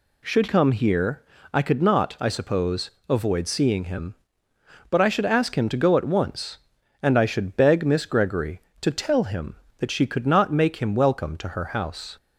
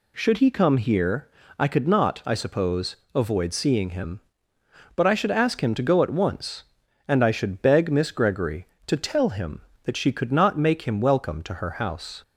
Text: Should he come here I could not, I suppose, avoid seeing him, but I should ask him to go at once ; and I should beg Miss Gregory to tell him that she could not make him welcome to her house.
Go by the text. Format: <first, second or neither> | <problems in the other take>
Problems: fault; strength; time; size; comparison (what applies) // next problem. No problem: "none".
second | skips "he"; at 0.4 s // pauses between "here" and "I"; slight; at 1.2 s; 0.30 s long; slight in the second